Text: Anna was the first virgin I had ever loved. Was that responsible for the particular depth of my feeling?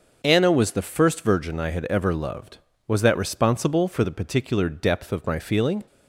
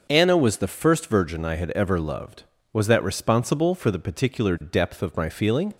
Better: neither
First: starts louder than the rest; until 1.2 s; 6 dB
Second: starts louder than the rest; until 1.1 s; 6 dB

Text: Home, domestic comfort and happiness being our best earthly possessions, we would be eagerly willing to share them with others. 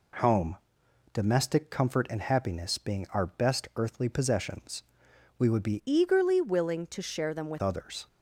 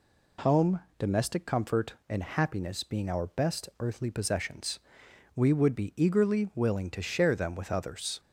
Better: second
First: changes voice from "eagerly" to "with"; from 5.8 to 7.6 s; 1.8 s long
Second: none

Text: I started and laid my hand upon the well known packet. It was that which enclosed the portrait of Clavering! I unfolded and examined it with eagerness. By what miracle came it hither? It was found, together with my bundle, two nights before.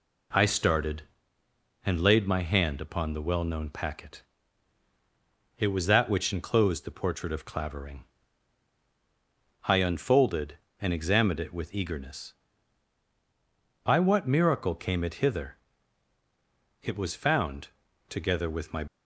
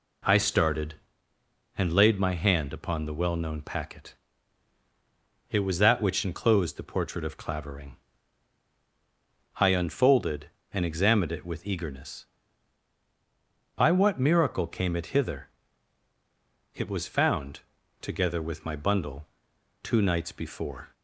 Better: second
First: stops before "bundle two nights before"; at 18.8 s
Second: none

